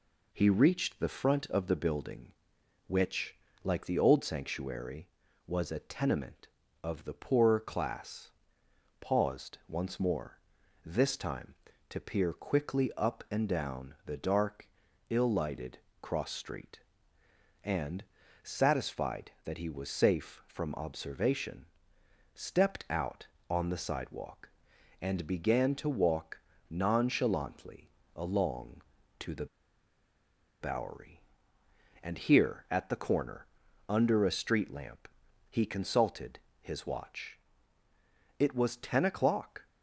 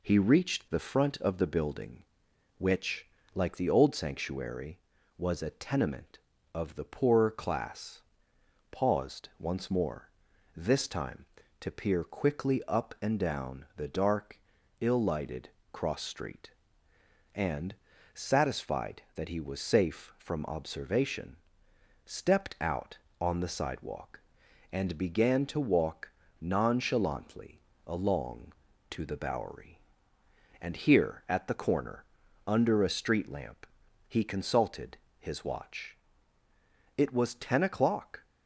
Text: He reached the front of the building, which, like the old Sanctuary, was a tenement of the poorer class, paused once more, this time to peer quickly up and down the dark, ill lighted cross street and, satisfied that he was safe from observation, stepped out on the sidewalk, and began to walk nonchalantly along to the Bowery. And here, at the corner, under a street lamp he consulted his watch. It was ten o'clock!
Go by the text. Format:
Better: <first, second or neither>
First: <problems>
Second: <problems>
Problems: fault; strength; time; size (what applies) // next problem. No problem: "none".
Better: second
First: pauses between "lighted" and "cross"; slight; at 15.7 s; 0.22 s long // pauses between "walk" and "nonchalantly"; slight; at 26.3 s; 0.32 s long // pauses between "nonchalantly" and "along"; slight; at 27.9 s; 0.24 s long // pauses between "the" and "Bowery"; at 29.4 s; 1.1 s long // pauses between "lamp" and "he"; at 35.0 s; 0.42 s long // pauses between "consulted" and "his"; slight; at 36.4 s; 0.20 s long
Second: pauses between "lighted" and "cross"; slight; at 15.4 s; 0.22 s long // pauses between "walk" and "nonchalantly"; slight; at 26.1 s; 0.32 s long // pauses between "nonchalantly" and "along"; slight; at 27.6 s; 0.24 s long // pauses between "lamp" and "he"; at 33.6 s; 0.42 s long // pauses between "consulted" and "his"; slight; at 34.9 s; 0.20 s long